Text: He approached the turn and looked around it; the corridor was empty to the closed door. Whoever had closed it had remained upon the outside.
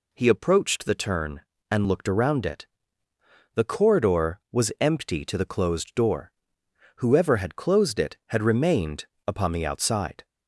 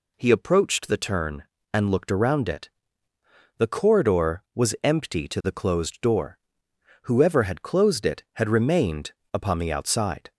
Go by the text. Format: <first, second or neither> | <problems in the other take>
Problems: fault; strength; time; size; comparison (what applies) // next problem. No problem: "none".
neither | pauses between "remained" and "upon"; slight; the same in both